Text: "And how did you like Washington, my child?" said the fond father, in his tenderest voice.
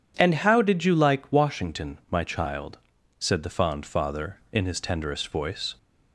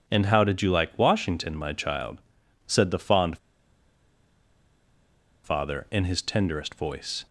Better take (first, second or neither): first